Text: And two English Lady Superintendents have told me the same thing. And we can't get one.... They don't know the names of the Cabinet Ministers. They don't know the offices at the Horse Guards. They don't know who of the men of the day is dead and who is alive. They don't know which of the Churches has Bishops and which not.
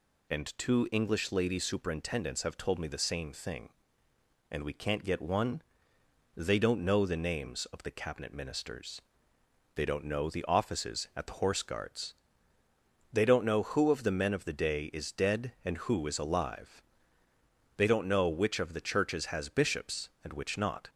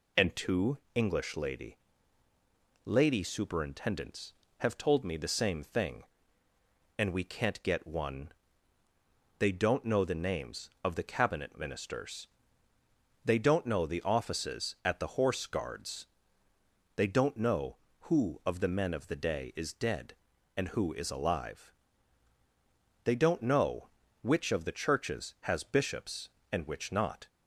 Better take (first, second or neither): first